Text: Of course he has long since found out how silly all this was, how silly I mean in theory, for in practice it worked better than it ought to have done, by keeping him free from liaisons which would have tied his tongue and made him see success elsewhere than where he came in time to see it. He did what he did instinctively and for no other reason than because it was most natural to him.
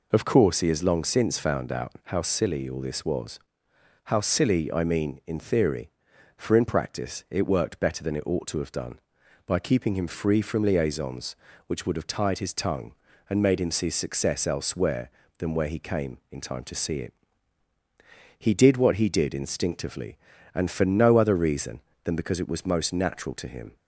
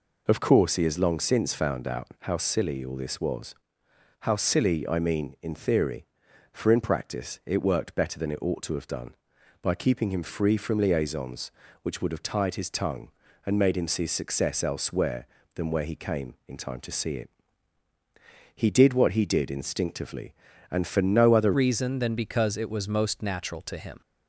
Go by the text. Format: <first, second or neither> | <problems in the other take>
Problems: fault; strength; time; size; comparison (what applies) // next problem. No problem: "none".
first | changes voice at "reason"; from 21.5 s on; 2.5 s long